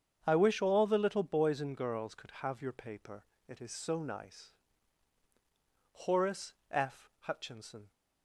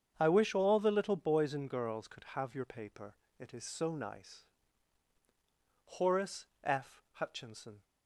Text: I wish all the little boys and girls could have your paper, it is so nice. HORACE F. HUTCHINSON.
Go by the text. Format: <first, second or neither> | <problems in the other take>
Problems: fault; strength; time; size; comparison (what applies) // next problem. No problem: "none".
neither | starts louder than the rest; strong; the same in both // pauses between "HORACE" and "F"; slight; the same in both